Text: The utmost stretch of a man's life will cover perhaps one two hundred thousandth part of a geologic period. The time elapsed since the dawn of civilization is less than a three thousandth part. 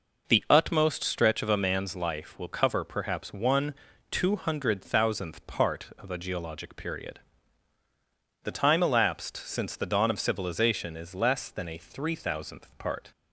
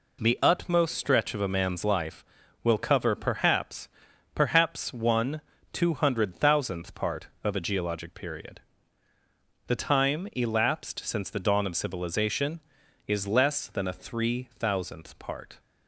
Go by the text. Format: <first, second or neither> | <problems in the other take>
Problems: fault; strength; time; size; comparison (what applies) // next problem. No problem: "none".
first | says "perhaps" twice; at 4.3 s // pauses between "one" and "two"; slight; at 5.3 s; 0.32 s long; slight in the first